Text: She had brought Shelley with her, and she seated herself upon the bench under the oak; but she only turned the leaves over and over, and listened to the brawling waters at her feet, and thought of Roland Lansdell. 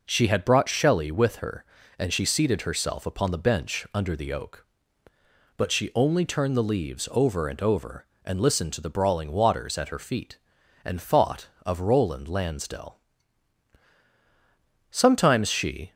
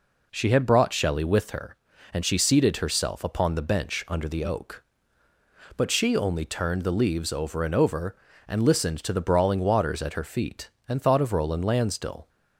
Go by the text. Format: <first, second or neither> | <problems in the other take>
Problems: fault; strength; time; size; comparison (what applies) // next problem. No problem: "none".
second | goes on to say "Sometimes she"; noticeable; from 14.9 s on; 1.0 s long